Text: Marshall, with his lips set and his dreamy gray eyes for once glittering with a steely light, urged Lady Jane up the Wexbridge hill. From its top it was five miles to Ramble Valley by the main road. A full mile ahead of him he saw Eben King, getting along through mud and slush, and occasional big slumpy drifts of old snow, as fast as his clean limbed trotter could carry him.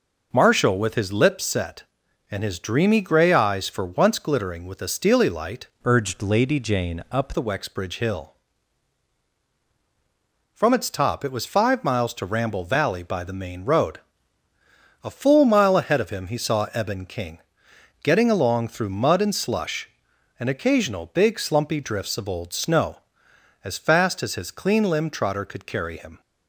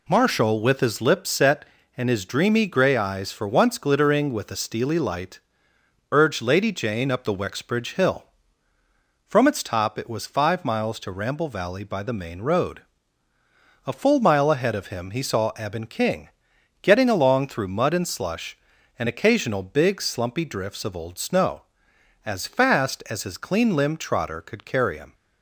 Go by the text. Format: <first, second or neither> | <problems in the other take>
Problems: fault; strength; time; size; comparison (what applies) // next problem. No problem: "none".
second | changes voice from "urged" to "up"; from 5.8 to 7.3 s; 1.5 s long